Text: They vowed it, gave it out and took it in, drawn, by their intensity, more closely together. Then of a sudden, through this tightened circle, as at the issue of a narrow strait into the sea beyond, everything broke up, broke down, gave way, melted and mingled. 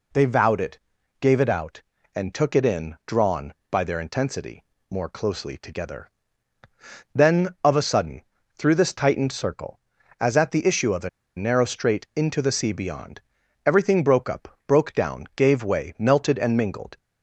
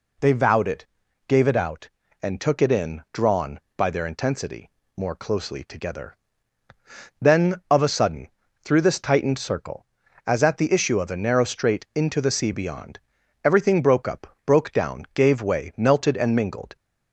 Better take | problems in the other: second | pauses between "a" and "narrow"; slight; at 11.0 s; 0.28 s long

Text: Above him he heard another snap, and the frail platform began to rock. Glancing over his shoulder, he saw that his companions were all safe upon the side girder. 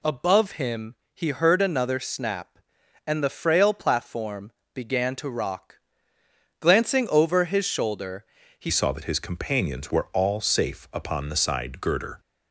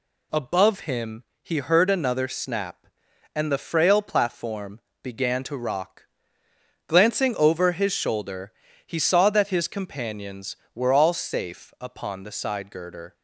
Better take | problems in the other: second | pauses between "him" and "he"; slight; at 0.9 s; 0.20 s long; slight in the second // pauses between "platform" and "began"; slight; at 4.5 s; 0.24 s long; slight in the second // changes voice at "saw"; from 8.6 s on; 3.5 s long

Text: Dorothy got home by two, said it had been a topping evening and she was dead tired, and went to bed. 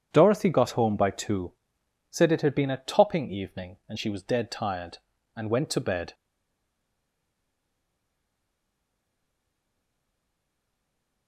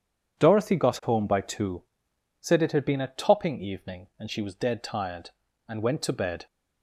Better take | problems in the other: second | stays silent after the last word; strong; from 6.1 s on; 5.1 s long

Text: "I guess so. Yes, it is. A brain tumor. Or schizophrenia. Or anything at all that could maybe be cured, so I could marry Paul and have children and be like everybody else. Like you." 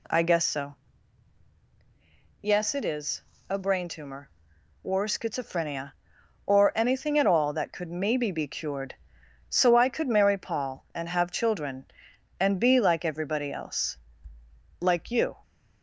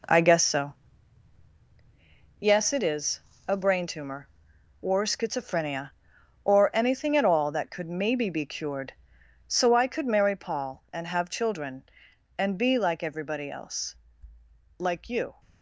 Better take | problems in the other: first | gets quieter; strong; throughout; 8.5 dB

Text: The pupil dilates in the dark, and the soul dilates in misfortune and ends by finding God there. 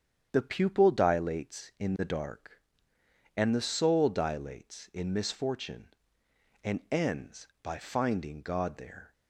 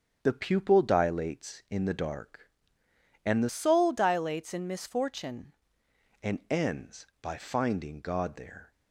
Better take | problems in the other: first | starts louder than the rest; until 1.2 s; 6.5 dB; strong in the first // changes voice from "soul" to "misfortune"; from 3.4 to 5.5 s; 2.1 s long

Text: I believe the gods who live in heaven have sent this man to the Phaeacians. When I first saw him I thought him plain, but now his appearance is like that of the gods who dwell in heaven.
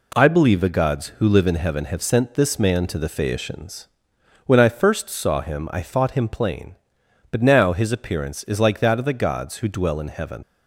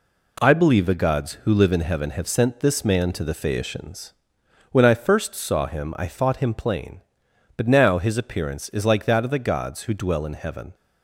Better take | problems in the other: second | leaves "heaven" unfinished; at 10.4 s; 60 ms

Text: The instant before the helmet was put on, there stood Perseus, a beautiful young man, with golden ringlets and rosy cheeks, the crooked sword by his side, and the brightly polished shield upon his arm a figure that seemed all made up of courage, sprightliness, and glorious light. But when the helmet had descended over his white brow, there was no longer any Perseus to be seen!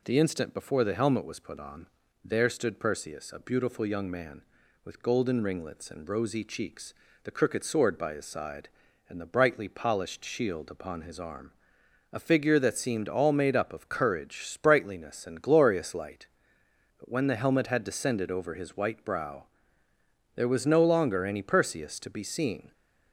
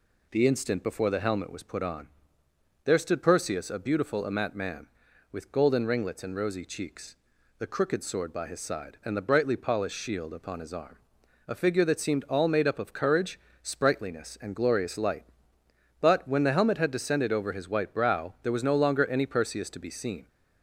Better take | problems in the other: first | says "amat" for "young"; at 4.2 s // pauses between "arm" and "a"; noticeable; at 10.9 s; 0.54 s long; noticeable in the first

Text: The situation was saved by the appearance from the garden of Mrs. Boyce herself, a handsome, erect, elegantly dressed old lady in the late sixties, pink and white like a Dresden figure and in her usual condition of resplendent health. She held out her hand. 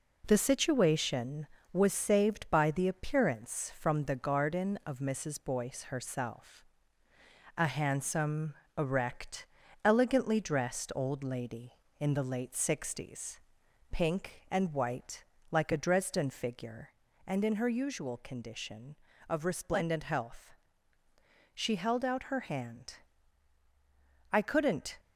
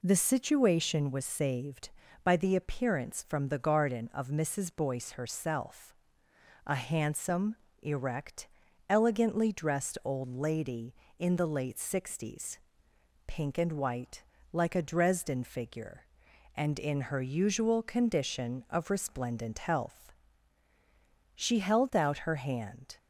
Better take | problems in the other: second | pauses between "white" and "like"; slight; at 15.2 s; 0.28 s long; slight in the second // goes on to say "I couldn't"; noticeable; from 24.3 s on; 0.68 s long

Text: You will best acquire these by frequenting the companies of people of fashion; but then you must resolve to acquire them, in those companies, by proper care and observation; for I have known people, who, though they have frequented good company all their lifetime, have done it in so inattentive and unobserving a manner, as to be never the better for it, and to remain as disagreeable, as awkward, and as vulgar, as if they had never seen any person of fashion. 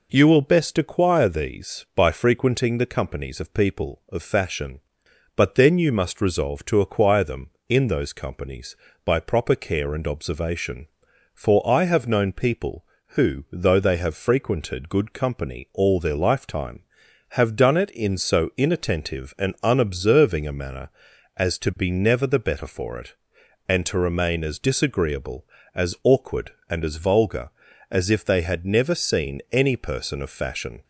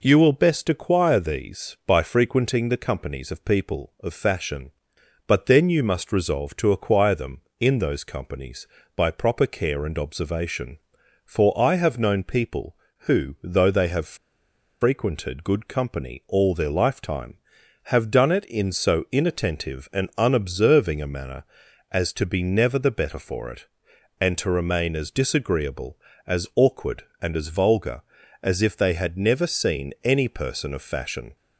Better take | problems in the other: first | pauses between "have" and "frequented"; noticeable; at 14.1 s; 0.63 s long

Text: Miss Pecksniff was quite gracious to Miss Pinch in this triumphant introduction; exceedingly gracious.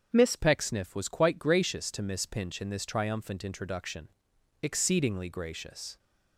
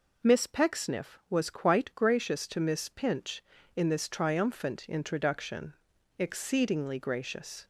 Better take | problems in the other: second | starts louder than the rest; strong; until 1.1 s; 7.5 dB // changes voice at "Pecksniff"; from 0.3 s on; 5.6 s long

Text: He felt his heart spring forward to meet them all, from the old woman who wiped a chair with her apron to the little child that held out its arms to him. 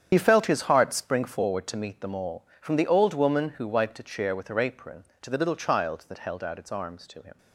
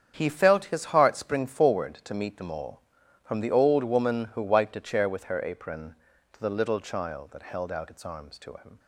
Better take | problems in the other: second | loses the start of "He"; at 0.1 s; 70 ms // starts louder than the rest; strong; until 1.1 s; 8.5 dB; strong in the second

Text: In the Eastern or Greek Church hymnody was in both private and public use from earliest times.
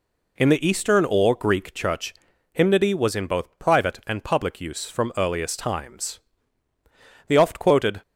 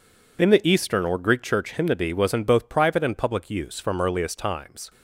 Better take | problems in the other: second | pauses between "Church" and "hymnody"; at 2.1 s; 0.40 s long // goes on to say "The oft quoted"; noticeable; from 7.2 s on; 0.74 s long

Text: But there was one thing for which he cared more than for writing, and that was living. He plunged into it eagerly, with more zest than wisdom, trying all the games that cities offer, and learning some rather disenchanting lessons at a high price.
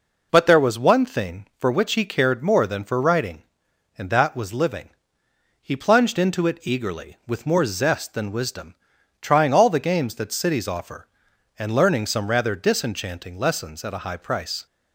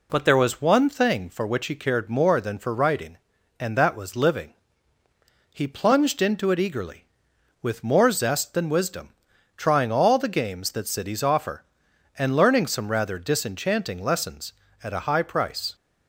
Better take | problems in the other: neither | none

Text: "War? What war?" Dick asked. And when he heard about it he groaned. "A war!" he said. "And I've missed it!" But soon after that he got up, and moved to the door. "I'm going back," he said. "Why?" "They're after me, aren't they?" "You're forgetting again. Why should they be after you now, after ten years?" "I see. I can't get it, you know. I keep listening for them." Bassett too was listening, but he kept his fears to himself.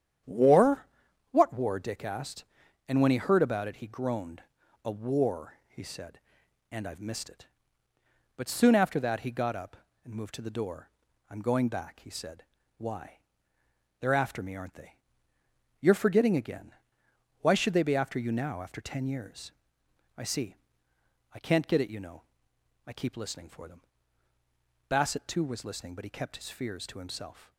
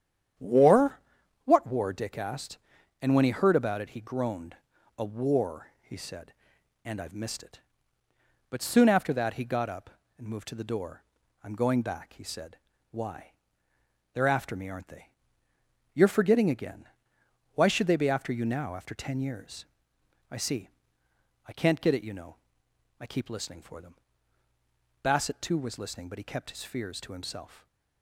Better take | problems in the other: neither | starts louder than the rest; strong; the same in both

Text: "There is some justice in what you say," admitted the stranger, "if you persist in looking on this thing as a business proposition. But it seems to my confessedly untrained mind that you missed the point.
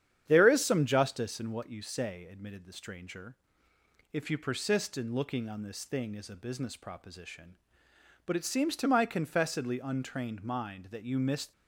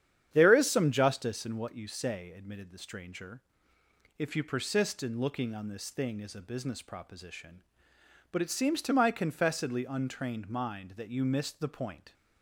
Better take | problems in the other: second | starts louder than the rest; strong; until 1.2 s; 9.5 dB; strong in the second // stops before "the point"; at 11.5 s

